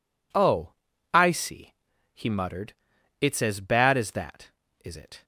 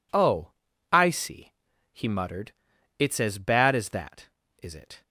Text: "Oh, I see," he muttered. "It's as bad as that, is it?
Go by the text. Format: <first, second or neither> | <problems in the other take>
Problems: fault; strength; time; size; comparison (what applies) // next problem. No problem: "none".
neither | none